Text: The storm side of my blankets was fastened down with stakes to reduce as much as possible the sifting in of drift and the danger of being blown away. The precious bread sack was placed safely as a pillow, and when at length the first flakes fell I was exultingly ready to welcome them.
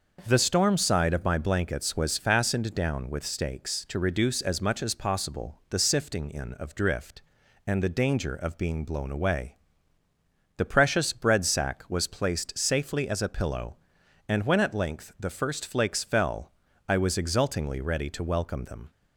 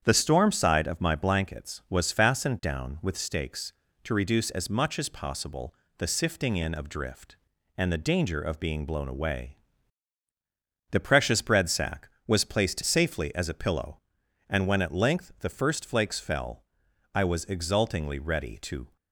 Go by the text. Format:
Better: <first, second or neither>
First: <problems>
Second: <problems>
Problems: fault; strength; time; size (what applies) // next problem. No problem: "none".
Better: first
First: pauses between "fell" and "I"; slight; at 16.5 s; 0.36 s long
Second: starts louder than the rest; strong; until 1.0 s; 8.5 dB // pauses between "possible" and "the"; slight; at 5.7 s; 0.24 s long // pauses between "fell" and "I"; noticeable; at 16.6 s; 0.50 s long // stops before "welcome them"; at 18.9 s